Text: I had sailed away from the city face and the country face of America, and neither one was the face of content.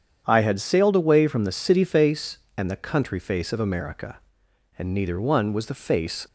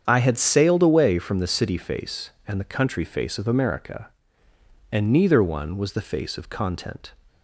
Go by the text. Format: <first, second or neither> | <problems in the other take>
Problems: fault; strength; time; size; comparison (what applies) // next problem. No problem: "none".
second | starts louder than the rest; strong; until 1.2 s; 8.5 dB; strong in the second // stops before "of content"; at 6.2 s